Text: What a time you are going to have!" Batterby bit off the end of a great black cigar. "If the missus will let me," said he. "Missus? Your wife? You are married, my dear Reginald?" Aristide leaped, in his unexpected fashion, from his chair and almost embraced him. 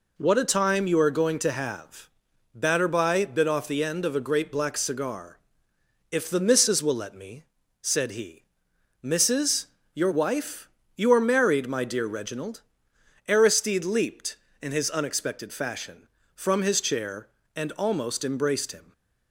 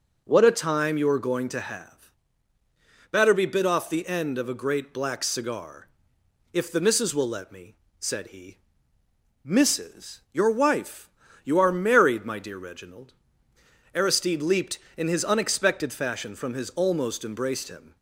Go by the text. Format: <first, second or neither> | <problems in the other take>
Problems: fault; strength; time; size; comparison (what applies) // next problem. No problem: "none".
first | skips "chair and"; at 16.6 s